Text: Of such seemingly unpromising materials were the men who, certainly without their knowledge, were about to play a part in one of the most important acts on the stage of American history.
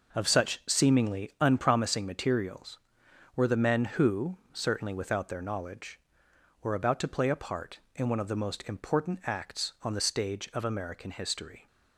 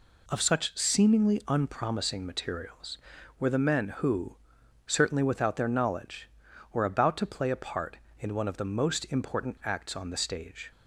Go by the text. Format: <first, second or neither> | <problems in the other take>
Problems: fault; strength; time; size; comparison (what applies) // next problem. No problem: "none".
first | stops before "of American history"; at 10.7 s